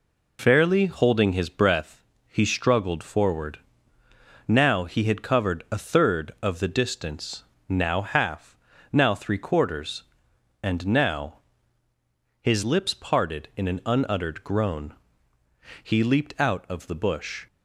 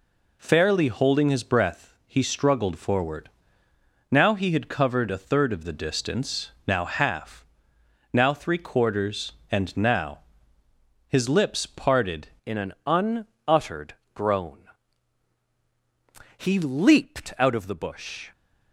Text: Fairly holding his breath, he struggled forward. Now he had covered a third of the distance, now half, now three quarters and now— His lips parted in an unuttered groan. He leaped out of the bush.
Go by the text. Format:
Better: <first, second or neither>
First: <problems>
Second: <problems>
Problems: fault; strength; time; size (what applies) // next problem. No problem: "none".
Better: first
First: none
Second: changes voice at "in"; from 12.4 s on; 5.9 s long // pauses between "unuttered" and "groan"; slight; at 13.9 s; 0.22 s long